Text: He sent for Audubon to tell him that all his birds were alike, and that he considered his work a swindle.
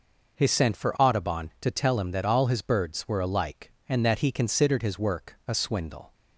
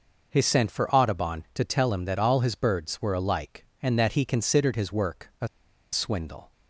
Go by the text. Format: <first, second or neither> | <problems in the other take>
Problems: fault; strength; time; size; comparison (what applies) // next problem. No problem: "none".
first | pauses between "a" and "swindle"; at 5.4 s; 0.45 s long